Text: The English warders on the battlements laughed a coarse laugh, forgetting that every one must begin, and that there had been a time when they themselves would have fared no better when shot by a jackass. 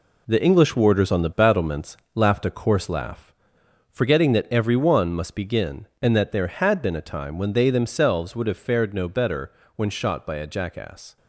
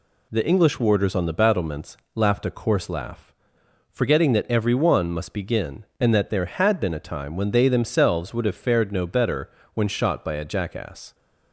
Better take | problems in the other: second | gets quieter; strong; throughout; 8 dB // pauses between "battlements" and "laughed"; slight; at 1.9 s; 0.18 s long; slight in the second // pauses between "better" and "when"; slight; at 9.5 s; 0.24 s long; slight in the second

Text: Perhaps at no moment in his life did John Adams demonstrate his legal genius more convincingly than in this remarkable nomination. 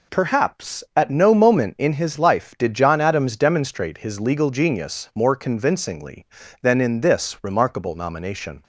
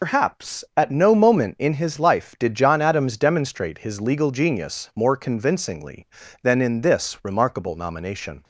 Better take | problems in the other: first | loses the start of "Perhaps"; at 0.0 s; 105 ms

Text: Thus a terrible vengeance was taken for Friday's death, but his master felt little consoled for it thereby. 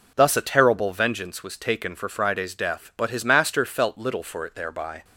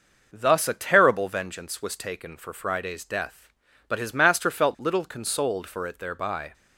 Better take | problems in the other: second | skips "consoled"; at 4.2 s

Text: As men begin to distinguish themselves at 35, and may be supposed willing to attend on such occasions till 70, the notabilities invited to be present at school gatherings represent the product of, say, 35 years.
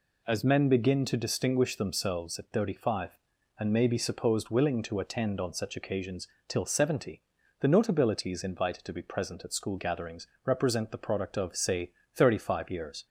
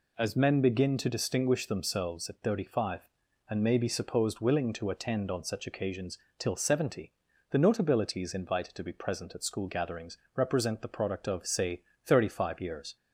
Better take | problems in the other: neither | pauses between "occasions" and "till"; slight; the same in both // pauses between "gatherings" and "represent"; slight; the same in both

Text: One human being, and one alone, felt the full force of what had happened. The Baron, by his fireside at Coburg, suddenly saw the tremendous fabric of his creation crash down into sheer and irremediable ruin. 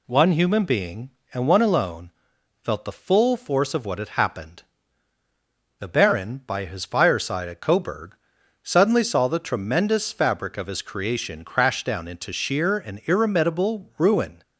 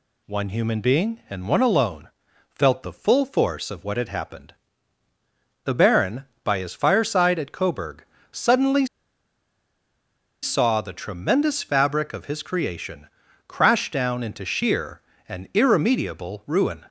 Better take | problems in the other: first | pauses between "suddenly" and "saw"; strong; at 8.8 s; 1.5 s long // pauses between "creation" and "crash"; at 13.0 s; 0.40 s long

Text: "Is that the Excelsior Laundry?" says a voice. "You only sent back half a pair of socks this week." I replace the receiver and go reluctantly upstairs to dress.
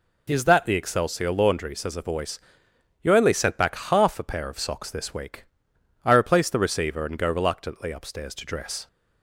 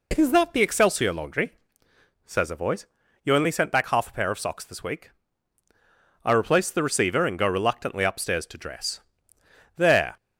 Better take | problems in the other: first | goes on to say "There"; slight; from 9.7 s on; 0.40 s long

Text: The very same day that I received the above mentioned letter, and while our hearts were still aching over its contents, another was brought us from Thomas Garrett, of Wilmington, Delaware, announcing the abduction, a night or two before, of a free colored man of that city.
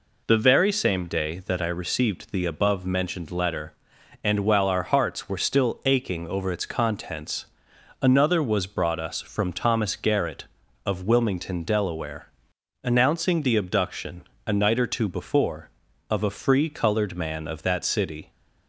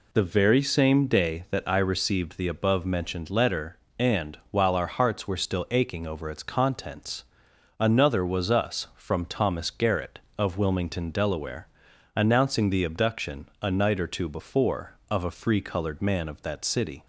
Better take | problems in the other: first | skips "brought"; at 8.5 s

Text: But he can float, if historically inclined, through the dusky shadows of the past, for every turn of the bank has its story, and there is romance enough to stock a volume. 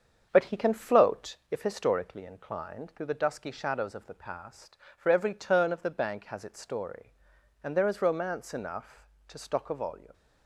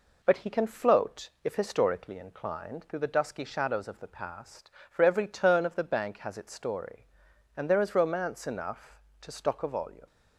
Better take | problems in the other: second | starts louder than the rest; strong; until 1.6 s; 7 dB

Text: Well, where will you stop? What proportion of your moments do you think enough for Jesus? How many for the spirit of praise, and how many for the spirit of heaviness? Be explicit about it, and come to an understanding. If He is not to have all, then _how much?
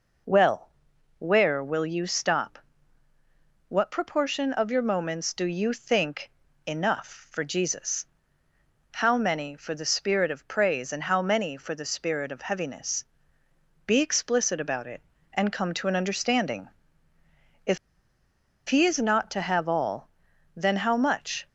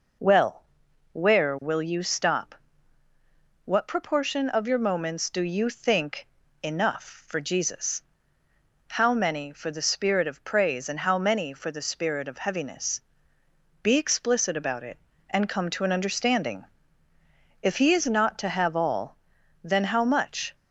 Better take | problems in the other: second | pauses between "think" and "enough"; slight; at 6.3 s; 0.34 s long; slight in the second // pauses between "If" and "He"; noticeable; at 17.7 s; 0.93 s long

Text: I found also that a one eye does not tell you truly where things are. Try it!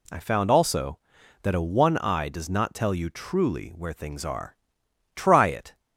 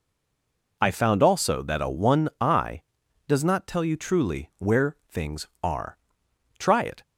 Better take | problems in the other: first | stays silent before the first word; slight; until 0.8 s; 0.8 s long

